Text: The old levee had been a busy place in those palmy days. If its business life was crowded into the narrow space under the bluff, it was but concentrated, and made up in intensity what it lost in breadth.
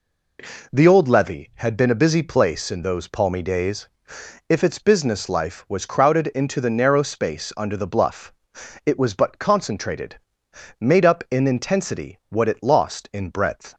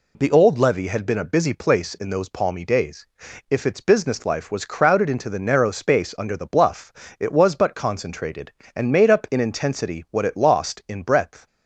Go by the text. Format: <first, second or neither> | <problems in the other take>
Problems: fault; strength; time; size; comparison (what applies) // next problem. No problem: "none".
second | skips "and"; at 10.4 s